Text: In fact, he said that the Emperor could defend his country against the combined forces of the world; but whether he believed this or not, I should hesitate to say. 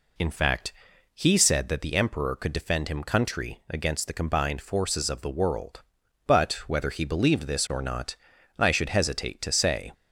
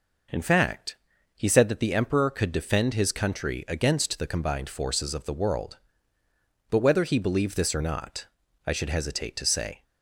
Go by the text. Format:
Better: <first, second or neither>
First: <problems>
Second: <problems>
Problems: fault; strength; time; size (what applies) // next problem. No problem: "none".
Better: second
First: says "him" for "his"; at 2.8 s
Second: none